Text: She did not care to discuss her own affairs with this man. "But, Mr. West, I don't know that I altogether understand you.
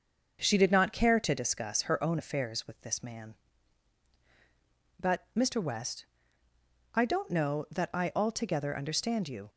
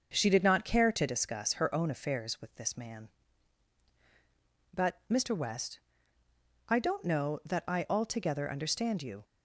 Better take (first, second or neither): neither